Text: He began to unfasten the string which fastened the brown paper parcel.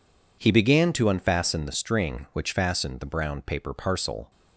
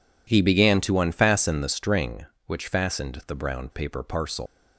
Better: first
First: none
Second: leaves "parcel" unfinished; at 4.4 s; 130 ms

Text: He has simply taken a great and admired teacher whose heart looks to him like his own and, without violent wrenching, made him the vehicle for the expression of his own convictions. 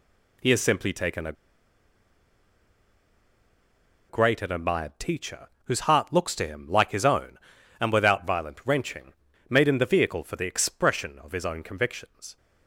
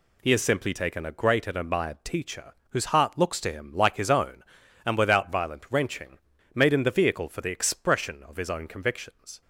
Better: second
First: pauses between "a" and "great"; strong; at 1.3 s; 2.7 s long // pauses between "teacher" and "whose"; slight; at 5.4 s; 0.16 s long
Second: pauses between "teacher" and "whose"; slight; at 2.5 s; 0.16 s long

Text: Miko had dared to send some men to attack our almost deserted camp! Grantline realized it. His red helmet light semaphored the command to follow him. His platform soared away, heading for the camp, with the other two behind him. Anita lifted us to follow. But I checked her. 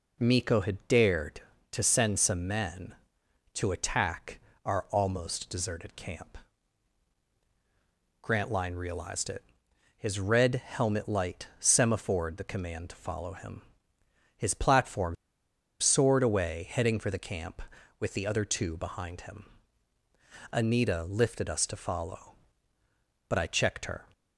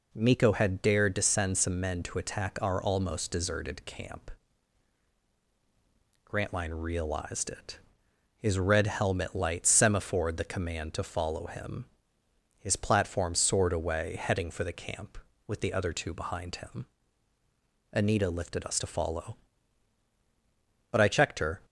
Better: second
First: pauses between "attack" and "our"; slight; at 4.4 s; 0.24 s long // pauses between "platform" and "soared"; noticeable; at 15.1 s; 0.65 s long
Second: none

